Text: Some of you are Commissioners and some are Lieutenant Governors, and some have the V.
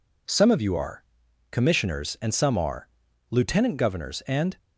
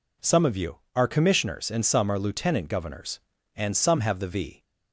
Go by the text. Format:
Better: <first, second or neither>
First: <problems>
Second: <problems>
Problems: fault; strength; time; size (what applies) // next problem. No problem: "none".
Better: second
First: pauses between "are" and "Commissioners"; noticeable; at 1.0 s; 0.48 s long // pauses between "are" and "Lieutenant"; at 2.8 s; 0.42 s long // stops before "some have the V"; at 4.5 s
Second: none